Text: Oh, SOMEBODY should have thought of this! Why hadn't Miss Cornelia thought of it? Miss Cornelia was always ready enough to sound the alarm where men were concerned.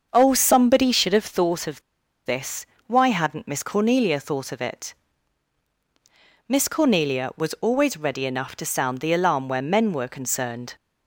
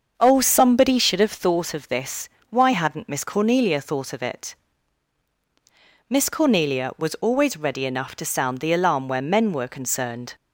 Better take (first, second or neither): second